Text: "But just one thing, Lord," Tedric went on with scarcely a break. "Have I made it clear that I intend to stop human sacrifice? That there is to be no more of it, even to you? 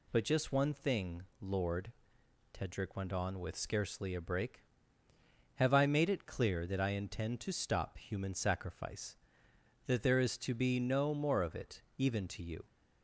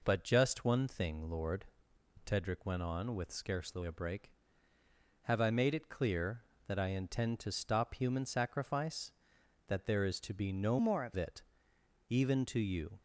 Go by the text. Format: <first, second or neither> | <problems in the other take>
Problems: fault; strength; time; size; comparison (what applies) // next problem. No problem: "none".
first | changes voice from "more" to "of"; from 10.7 to 11.1 s; 0.4 s long